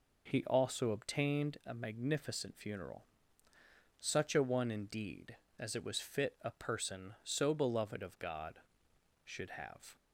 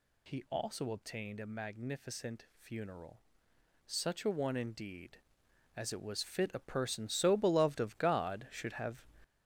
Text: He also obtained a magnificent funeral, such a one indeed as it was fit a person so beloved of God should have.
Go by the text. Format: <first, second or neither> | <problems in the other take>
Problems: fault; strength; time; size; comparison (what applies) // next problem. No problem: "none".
first | gets louder; strong; throughout; 7 dB